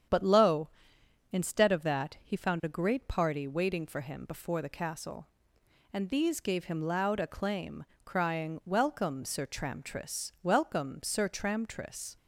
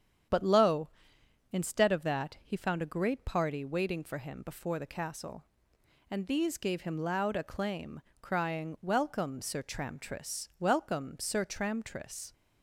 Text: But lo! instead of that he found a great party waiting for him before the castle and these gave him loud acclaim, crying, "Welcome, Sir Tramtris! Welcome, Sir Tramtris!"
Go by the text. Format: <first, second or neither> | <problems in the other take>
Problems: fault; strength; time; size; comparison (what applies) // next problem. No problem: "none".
neither | starts louder than the rest; strong; the same in both